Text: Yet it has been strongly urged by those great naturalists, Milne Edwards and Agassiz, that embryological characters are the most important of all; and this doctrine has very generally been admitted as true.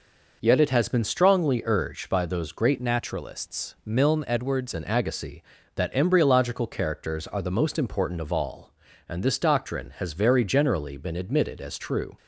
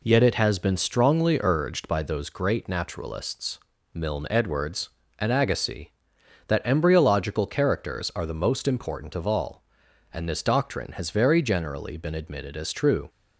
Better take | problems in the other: second | changes voice from "naturalists" to "Edwards"; from 2.7 to 4.7 s; 2.0 s long

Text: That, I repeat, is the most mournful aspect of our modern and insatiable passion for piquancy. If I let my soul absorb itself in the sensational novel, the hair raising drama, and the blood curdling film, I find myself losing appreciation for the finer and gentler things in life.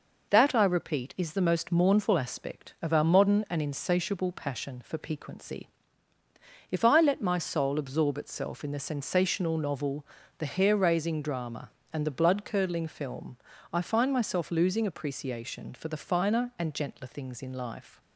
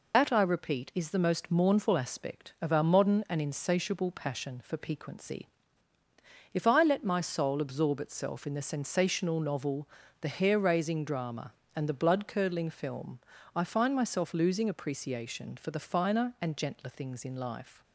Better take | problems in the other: first | loses the start of "That"; at 0.1 s; 70 ms

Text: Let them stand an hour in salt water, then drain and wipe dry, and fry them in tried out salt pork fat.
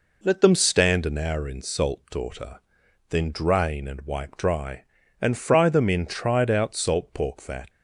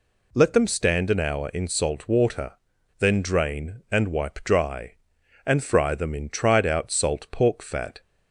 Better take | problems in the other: second | says "daughter" for "water"; at 2.1 s

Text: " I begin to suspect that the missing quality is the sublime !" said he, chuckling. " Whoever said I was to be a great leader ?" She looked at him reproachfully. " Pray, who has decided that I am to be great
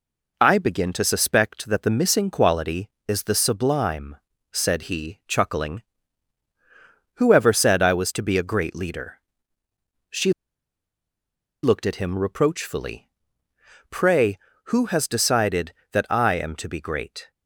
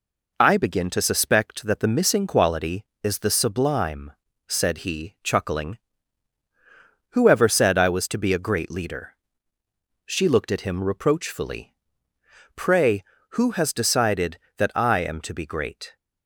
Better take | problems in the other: second | pauses between "She" and "looked"; strong; at 10.3 s; 1.3 s long

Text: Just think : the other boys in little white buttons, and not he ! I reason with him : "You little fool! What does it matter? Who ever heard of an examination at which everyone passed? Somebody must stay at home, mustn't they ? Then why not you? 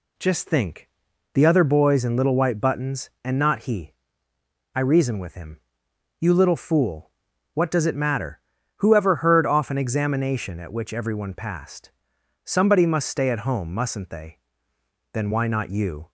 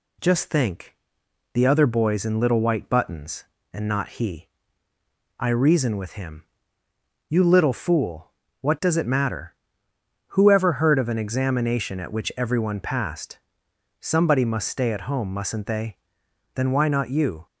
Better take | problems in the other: second | says "off" for "of"; at 9.4 s

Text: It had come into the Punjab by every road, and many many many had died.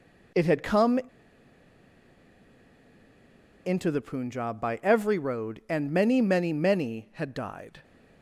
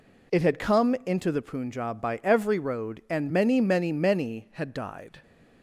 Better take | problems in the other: second | pauses between "come" and "into"; strong; at 0.9 s; 2.6 s long

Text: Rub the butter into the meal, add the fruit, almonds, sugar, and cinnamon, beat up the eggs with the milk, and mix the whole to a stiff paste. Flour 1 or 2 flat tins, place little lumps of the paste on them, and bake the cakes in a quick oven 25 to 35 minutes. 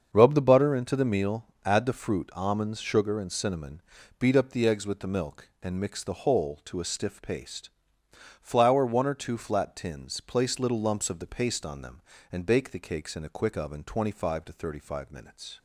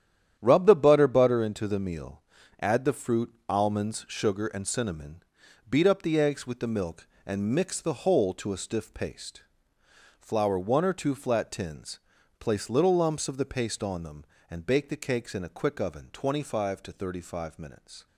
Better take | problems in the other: first | starts louder than the rest; strong; until 1.4 s; 10 dB; also in the first // says "butter" twice; at 1.0 s

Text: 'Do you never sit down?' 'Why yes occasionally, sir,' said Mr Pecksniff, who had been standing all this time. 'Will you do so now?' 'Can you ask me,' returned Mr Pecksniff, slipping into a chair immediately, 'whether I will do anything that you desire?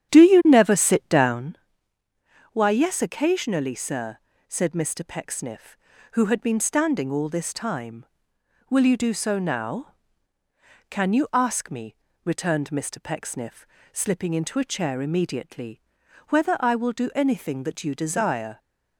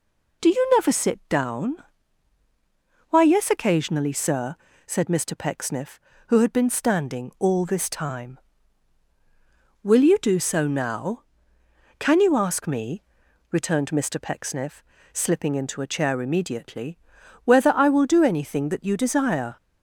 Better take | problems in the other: second | starts louder than the rest; strong; until 1.6 s; 9.5 dB

